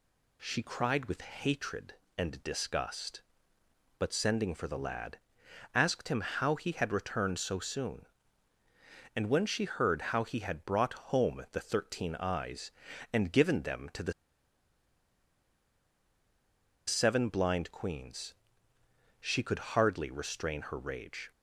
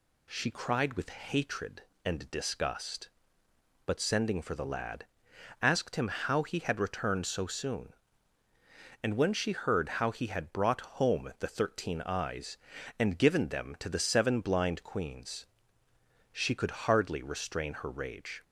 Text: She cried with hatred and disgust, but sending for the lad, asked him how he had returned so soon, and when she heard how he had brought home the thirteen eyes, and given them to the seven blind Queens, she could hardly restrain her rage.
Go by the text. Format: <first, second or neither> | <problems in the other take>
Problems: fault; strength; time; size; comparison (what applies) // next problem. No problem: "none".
second | pauses between "the" and "seven"; strong; at 14.1 s; 2.7 s long